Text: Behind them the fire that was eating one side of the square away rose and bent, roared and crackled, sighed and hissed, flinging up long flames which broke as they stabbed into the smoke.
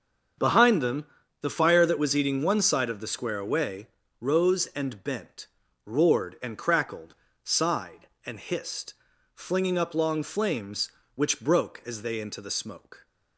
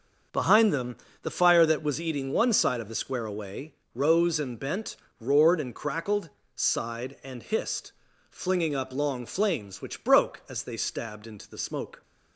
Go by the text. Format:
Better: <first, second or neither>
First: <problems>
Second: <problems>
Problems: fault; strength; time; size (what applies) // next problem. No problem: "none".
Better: second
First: starts louder than the rest; until 1.7 s; 7 dB // pauses between "them" and "the"; slight; at 1.0 s; 0.36 s long // pauses between "away" and "rose"; slight; at 3.8 s; 0.34 s long // skips "stabbed"; at 12.2 s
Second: starts louder than the rest; until 1.5 s; 6.5 dB // pauses between "them" and "the"; slight; at 0.9 s; 0.26 s long // pauses between "away" and "rose"; slight; at 3.7 s; 0.20 s long